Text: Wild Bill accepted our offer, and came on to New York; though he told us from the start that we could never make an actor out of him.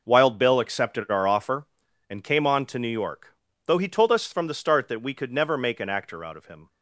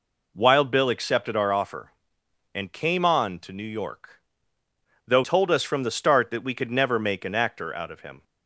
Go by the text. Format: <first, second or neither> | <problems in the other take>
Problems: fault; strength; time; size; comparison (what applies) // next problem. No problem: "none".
first | skips "he"; at 5.2 s